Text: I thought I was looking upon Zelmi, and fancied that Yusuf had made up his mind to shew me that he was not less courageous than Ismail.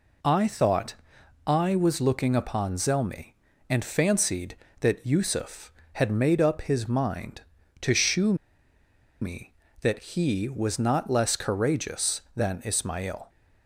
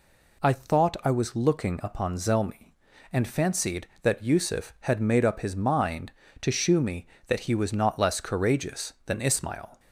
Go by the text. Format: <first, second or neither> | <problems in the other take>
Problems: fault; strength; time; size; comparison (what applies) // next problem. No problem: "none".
second | pauses between "thought" and "I"; noticeable; at 0.9 s; 0.54 s long // pauses between "shew" and "me"; noticeable; at 8.3 s; 0.87 s long